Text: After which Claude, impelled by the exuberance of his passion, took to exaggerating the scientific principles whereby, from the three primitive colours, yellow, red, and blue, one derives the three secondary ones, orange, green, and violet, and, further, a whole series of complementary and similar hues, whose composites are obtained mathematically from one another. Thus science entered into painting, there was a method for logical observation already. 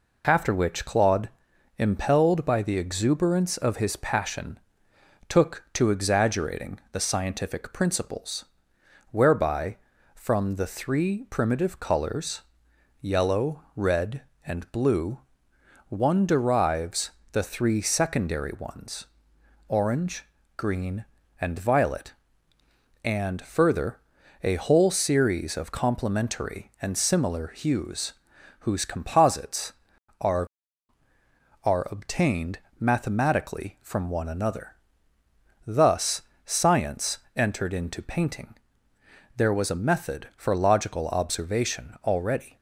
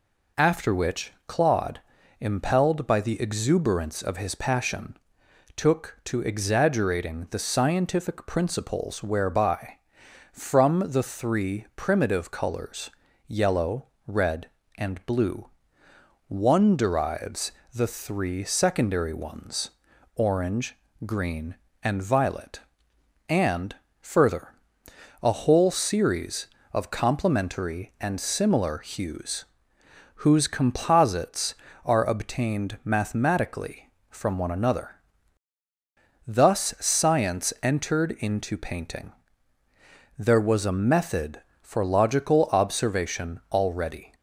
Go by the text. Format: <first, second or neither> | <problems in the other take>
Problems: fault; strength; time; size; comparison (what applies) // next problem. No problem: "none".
second | pauses between "principles" and "whereby"; noticeable; at 8.4 s; 0.68 s long // pauses between "derives" and "the"; slight; at 17.1 s; 0.20 s long; slight in the second // says "are" twice; at 31.6 s // pauses between "obtained" and "mathematically"; slight; at 32.5 s; 0.22 s long // pauses between "Thus" and "science"; slight; at 36.2 s; 0.22 s long // pauses between "science" and "entered"; slight; at 37.1 s; 0.18 s long